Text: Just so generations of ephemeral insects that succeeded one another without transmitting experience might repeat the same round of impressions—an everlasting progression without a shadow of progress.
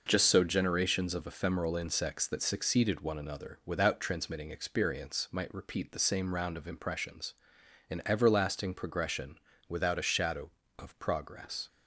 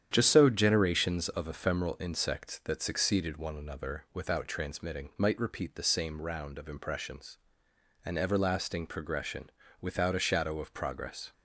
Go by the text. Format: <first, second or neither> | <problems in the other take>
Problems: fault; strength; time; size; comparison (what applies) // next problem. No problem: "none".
first | starts louder than the rest; strong; until 1.1 s; 9.5 dB // skips "experience"; at 5.1 s // pauses between "progression" and "without"; slight; at 9.4 s; 0.32 s long; slight in the first